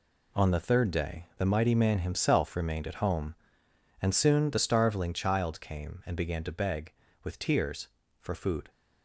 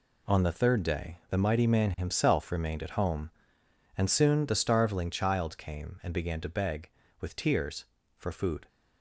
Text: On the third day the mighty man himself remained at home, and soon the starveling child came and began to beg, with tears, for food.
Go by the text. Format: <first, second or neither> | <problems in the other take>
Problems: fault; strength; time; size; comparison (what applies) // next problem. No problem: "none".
neither | none